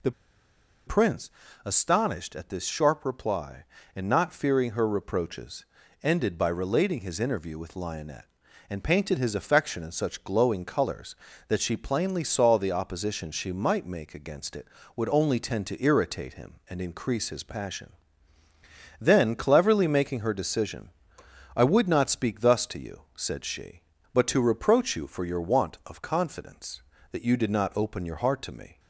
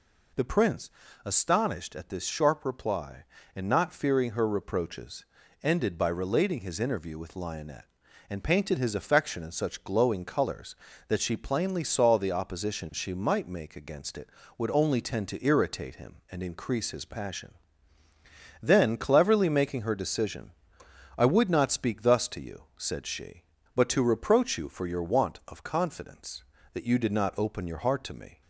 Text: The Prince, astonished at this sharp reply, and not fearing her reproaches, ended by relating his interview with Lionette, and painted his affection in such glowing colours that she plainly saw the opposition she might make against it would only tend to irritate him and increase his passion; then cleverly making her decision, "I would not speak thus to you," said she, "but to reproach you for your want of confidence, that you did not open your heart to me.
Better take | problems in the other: second | pauses between "The" and "Prince"; noticeable; at 0.1 s; 0.74 s long

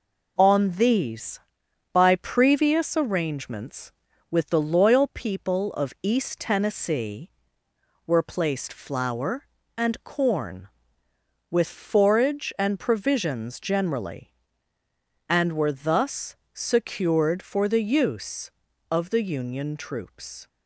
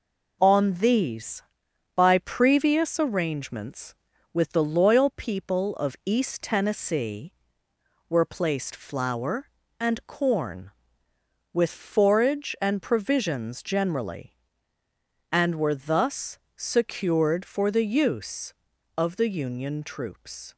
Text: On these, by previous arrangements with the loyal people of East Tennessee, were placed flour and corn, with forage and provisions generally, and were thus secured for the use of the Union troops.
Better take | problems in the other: neither | pauses between "thus" and "secured"; slight; the same in both

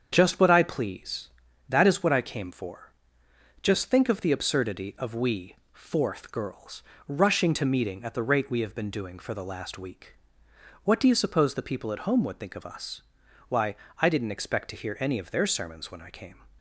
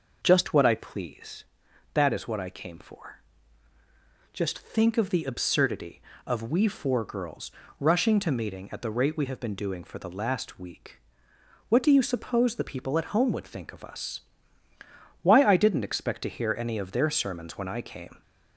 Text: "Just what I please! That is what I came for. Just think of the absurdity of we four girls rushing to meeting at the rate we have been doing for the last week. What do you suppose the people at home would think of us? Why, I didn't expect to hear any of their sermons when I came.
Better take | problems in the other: second | starts louder than the rest; strong; until 1.1 s; 7.5 dB // says "fourth" for "four"; at 5.7 s // pauses between "girls" and "rushing"; slight; at 6.8 s; 0.24 s long; slight in the second

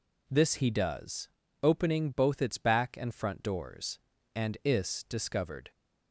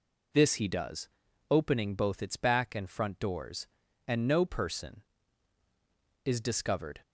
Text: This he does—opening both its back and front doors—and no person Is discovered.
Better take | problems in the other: second | skips "no person"; at 4.6 s

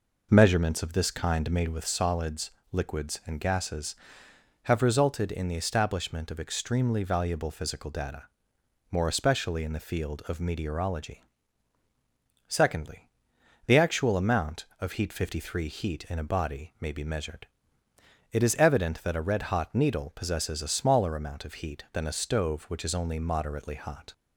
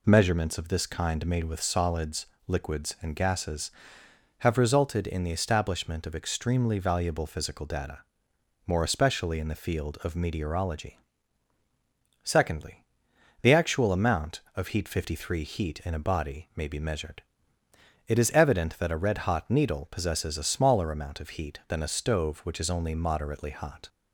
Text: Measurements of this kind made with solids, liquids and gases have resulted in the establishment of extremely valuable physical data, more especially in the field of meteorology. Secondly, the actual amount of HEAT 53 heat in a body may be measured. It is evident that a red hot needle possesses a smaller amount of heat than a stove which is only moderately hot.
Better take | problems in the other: second | starts louder than the rest; noticeable; until 1.8 s; 5 dB

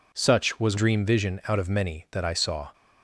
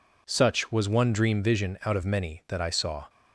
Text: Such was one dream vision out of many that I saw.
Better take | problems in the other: second | skips "one"; at 0.7 s

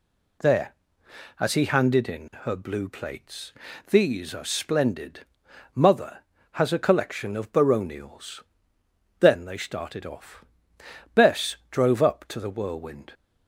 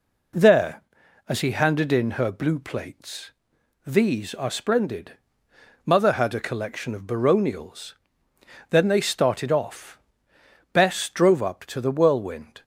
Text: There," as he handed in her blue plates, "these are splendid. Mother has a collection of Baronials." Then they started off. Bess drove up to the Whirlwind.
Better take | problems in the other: first | says "had" for "has"; at 6.1 s

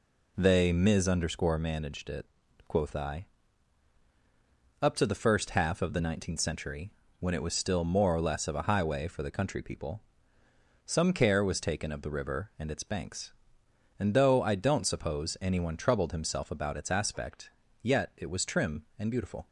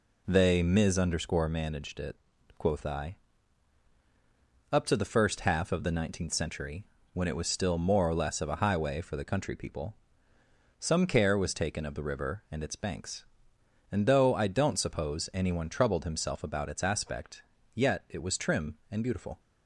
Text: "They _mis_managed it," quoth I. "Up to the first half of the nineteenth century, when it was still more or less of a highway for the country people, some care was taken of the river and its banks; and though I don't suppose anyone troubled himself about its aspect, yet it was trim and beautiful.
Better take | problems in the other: neither | none

